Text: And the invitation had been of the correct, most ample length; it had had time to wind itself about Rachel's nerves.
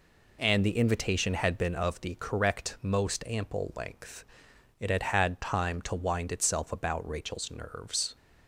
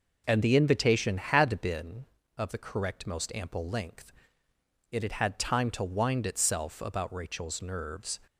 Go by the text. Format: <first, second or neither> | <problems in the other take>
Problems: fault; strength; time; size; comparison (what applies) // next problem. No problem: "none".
first | starts louder than the rest; noticeable; until 1.9 s; 5 dB